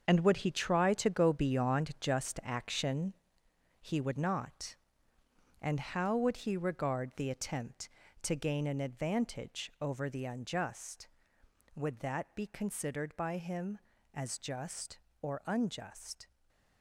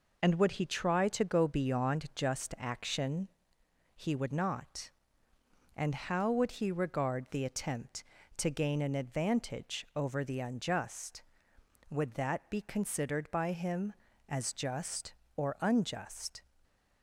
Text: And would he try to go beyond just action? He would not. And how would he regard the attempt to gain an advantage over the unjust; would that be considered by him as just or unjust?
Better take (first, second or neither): second